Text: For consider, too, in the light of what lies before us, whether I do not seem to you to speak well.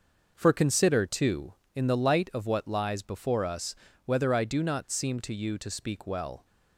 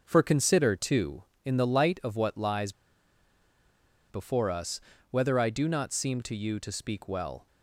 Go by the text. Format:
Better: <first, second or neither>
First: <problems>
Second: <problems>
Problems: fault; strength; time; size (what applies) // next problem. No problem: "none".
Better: first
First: none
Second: pauses between "lies" and "before"; strong; at 2.7 s; 1.3 s long